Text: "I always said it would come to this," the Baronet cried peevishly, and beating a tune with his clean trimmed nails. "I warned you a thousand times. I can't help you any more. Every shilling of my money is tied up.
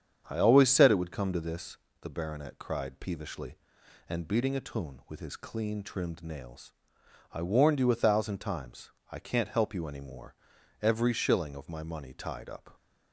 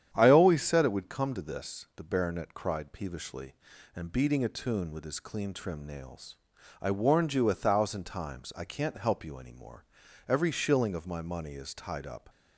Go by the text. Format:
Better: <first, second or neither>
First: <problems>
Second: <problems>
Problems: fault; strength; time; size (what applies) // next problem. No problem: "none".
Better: second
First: starts louder than the rest; strong; until 1.2 s; 8 dB // skips "is"; at 12.1 s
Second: starts louder than the rest; strong; until 1.1 s; 9 dB